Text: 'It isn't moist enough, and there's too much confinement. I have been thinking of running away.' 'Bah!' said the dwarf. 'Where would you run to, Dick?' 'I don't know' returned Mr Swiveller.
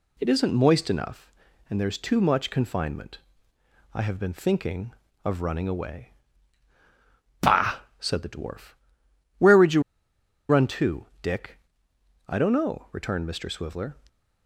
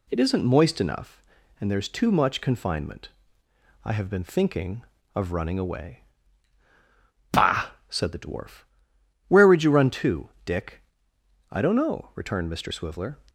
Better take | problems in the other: second | pauses between "you" and "run"; noticeable; at 9.8 s; 0.68 s long

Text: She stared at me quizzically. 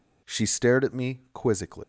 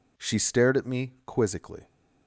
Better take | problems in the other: second | leaves "quizzically" unfinished; at 1.8 s; 115 ms

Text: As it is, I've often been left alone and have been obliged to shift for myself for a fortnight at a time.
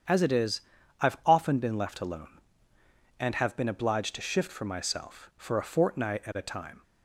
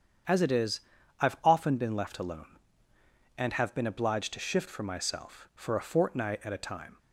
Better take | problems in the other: neither | starts louder than the rest; strong; the same in both

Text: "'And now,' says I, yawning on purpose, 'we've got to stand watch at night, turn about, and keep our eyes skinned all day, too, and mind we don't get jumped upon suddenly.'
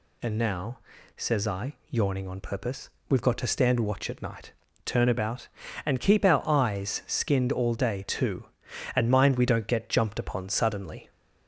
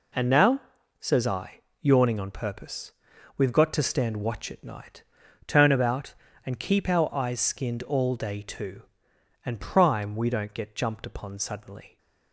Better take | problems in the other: first | says "prime" for "mind"; at 9.5 s

